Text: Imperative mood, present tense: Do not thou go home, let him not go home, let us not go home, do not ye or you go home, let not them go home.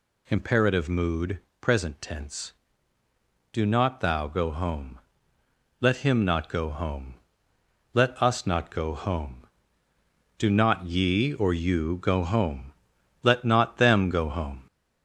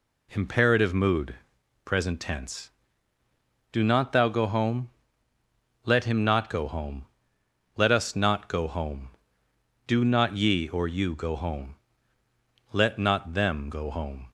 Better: second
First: gets louder; slight; throughout; 2.5 dB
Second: none

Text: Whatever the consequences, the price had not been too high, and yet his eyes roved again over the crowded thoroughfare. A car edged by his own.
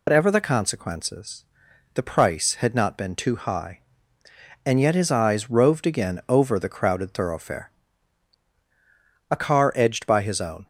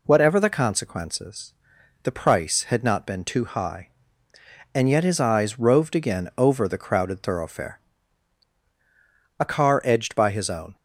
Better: second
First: loses the start of "Whatever"; at 0.0 s; 105 ms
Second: none

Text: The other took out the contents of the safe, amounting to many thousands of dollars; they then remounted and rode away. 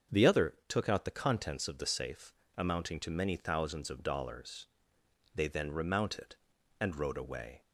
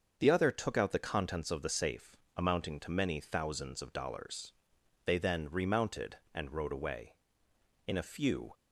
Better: first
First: starts louder than the rest; until 1.2 s; 6.5 dB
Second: starts louder than the rest; until 1.1 s; 6.5 dB // goes on to say "In a few"; noticeable; from 7.8 s on; 0.66 s long

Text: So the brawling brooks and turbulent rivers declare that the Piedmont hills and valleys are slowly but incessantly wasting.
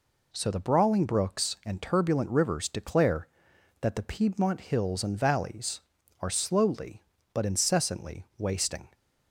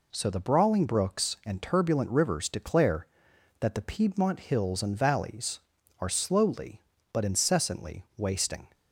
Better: neither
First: none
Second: none

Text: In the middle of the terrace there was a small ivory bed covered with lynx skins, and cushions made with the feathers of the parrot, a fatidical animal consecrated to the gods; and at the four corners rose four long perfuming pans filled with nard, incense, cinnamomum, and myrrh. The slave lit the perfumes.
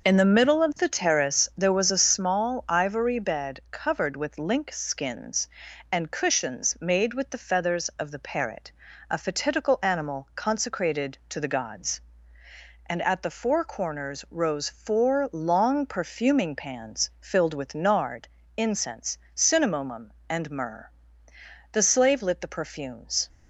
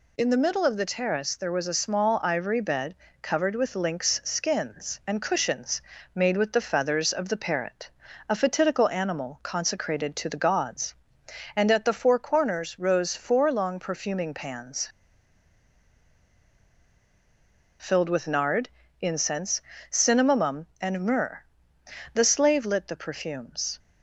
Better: first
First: none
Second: pauses between "bed" and "covered"; slight; at 2.9 s; 0.28 s long // pauses between "cushions" and "made"; slight; at 5.7 s; 0.34 s long // pauses between "pans" and "filled"; strong; at 14.8 s; 2.9 s long

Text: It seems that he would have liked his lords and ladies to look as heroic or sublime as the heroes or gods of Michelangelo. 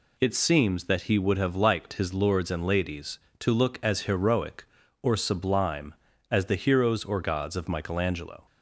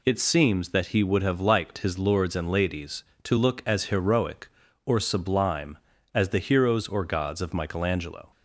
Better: neither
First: none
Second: none

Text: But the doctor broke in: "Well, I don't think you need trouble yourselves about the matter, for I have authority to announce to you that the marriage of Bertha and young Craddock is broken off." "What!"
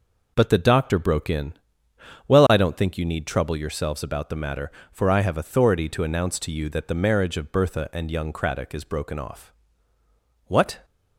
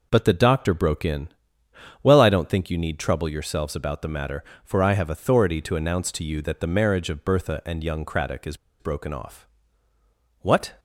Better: first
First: none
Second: pauses between "is" and "broken"; slight; at 8.5 s; 0.22 s long

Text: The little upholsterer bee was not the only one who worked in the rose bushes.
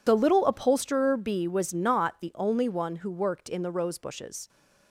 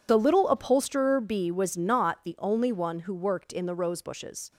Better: neither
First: none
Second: none

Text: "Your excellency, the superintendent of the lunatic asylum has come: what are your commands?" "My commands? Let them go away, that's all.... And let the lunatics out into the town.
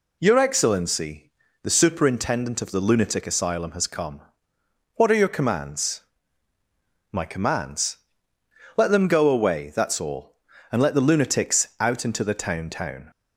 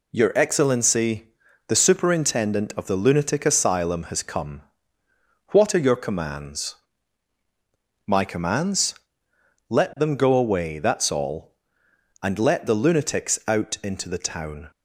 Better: second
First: says "town" twice; at 12.6 s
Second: none

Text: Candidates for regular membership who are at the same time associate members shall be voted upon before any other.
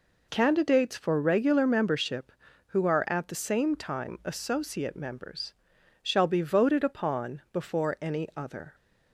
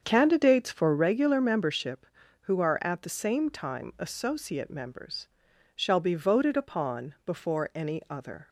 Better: first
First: pauses between "members" and "shall"; noticeable; at 5.5 s; 0.50 s long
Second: starts louder than the rest; strong; until 1.1 s; 7 dB // pauses between "members" and "shall"; noticeable; at 5.2 s; 0.48 s long

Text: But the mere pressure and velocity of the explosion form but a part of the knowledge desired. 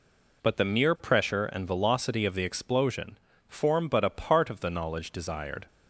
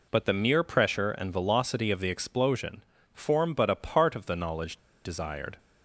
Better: first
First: pauses between "explosion" and "form"; slight; at 3.1 s; 0.30 s long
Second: pauses between "explosion" and "form"; slight; at 2.8 s; 0.30 s long // pauses between "knowledge" and "desired"; slight; at 4.7 s; 0.26 s long

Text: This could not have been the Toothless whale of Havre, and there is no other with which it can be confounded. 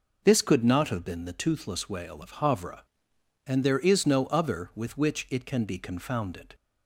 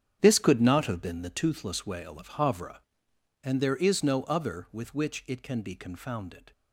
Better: first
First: none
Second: gets quieter; strong; throughout; 12.5 dB

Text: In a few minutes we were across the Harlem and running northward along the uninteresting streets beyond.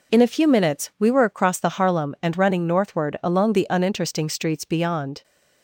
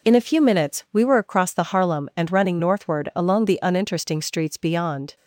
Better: neither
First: none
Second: none

